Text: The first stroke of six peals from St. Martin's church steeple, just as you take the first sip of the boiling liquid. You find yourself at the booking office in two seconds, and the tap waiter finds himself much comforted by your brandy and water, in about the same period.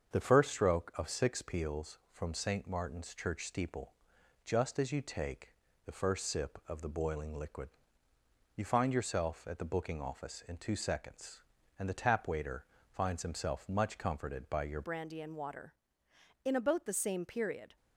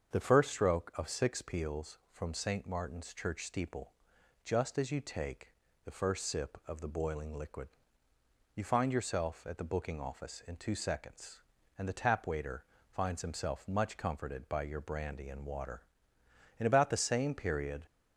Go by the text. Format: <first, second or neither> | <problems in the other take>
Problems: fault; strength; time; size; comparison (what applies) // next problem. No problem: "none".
second | starts louder than the rest; until 1.1 s; 7 dB; also in the second // pauses between "take" and "the"; slight; at 5.5 s; 0.32 s long; slight in the second // pauses between "waiter" and "finds"; slight; at 12.6 s; 0.24 s long; slight in the second // changes voice at "brandy"; from 14.8 s on; 2.9 s long